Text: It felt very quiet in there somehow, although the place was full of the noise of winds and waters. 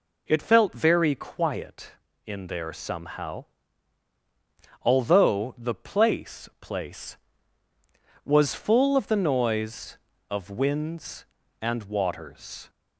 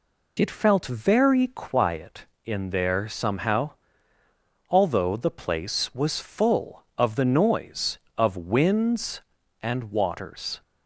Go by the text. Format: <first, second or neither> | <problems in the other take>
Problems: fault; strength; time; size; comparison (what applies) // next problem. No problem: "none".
second | says "place" twice; at 6.5 s